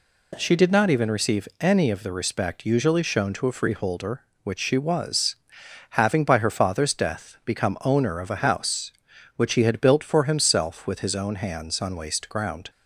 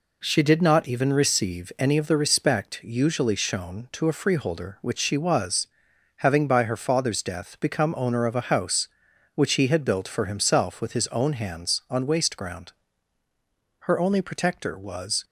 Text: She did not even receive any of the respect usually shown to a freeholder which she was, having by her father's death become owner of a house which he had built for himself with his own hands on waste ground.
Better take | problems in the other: first | goes on to say "Her only protector was"; from 13.7 s on; 1.4 s long

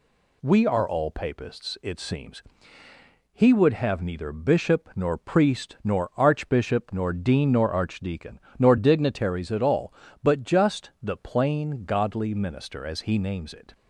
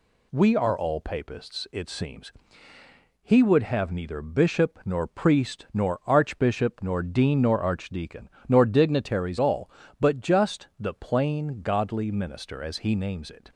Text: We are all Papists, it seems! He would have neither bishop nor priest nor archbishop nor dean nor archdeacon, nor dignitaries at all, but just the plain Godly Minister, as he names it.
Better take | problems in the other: first | skips "at"; at 9.3 s

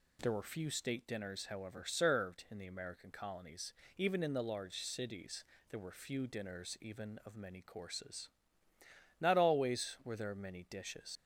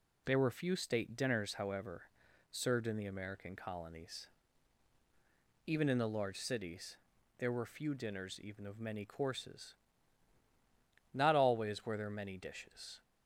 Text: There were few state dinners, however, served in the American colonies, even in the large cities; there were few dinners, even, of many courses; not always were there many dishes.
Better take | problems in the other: second | leaves "dishes" unfinished; at 11.1 s; 90 ms

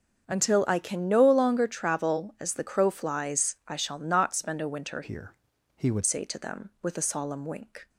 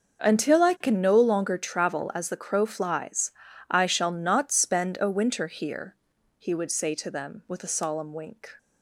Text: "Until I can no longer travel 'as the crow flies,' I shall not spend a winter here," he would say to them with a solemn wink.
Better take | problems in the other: second | starts louder than the rest; until 1.2 s; 6.5 dB; noticeable in the second // changes voice from "here" to "would"; from 5.0 to 6.0 s; 1.0 s long

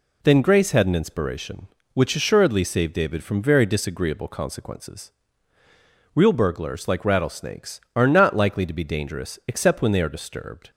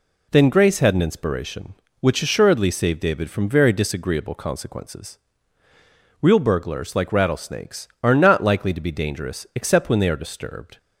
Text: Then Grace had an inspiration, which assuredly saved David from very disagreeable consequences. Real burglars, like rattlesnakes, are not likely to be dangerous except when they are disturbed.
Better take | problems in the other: neither | none

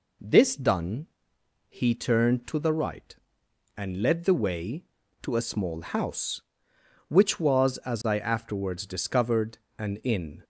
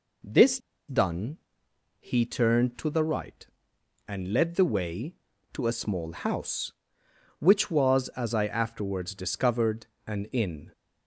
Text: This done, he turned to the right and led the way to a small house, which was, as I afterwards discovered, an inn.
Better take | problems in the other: first | pauses between "This" and "done"; slight; at 0.5 s; 0.30 s long

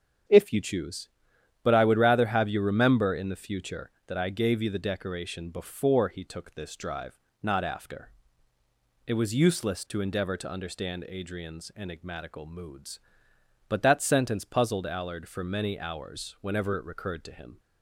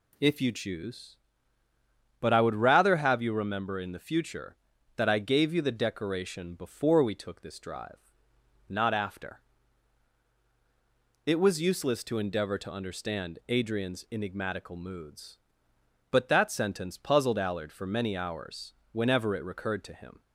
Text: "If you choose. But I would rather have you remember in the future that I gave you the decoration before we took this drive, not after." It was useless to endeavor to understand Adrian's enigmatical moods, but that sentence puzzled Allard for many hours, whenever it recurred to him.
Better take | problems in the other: second | starts louder than the rest; strong; until 1.8 s; 8 dB // says "he" for "we"; at 6.0 s

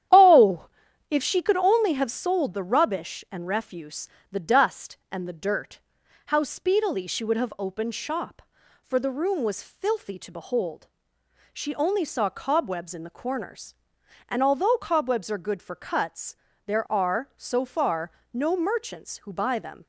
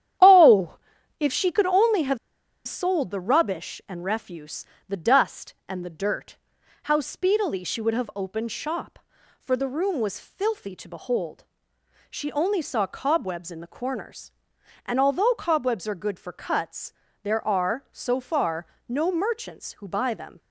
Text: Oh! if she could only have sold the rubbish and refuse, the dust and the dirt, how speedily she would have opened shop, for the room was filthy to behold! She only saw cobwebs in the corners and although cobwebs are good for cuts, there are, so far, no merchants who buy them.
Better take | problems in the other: first | starts louder than the rest; strong; until 1.6 s; 10.5 dB; strong in the first // pauses between "have" and "sold"; noticeable; at 2.1 s; 0.49 s long

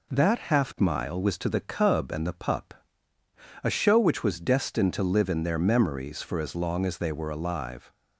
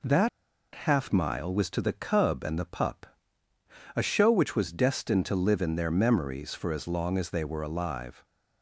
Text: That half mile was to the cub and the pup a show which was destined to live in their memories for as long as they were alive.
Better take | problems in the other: first | pauses between "That" and "half"; at 0.2 s; 0.45 s long // pauses between "pup" and "a"; noticeable; at 3.0 s; 0.90 s long; noticeable in the first

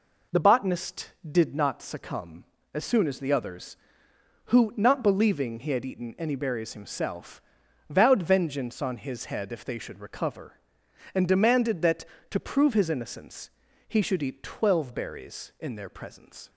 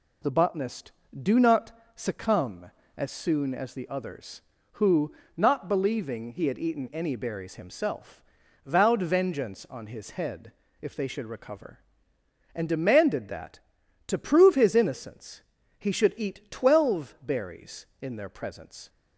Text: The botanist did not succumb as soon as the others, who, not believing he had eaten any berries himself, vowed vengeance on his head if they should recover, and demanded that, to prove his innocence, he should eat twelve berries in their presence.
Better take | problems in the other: first | says "do" for "did"; at 1.2 s // pauses between "not" and "succumb"; slight; at 1.7 s; 0.22 s long // pauses between "head" and "if"; slight; at 10.5 s; 0.28 s long

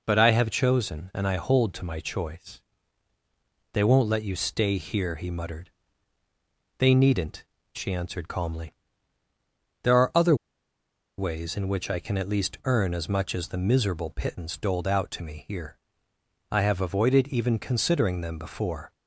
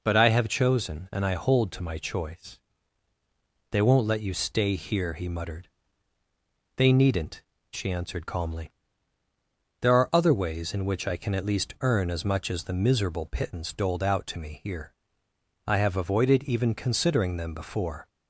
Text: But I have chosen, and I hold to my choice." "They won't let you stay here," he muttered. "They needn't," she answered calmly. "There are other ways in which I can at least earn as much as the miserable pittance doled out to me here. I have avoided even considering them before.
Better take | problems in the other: second | pauses between "other" and "ways"; noticeable; at 10.3 s; 0.82 s long

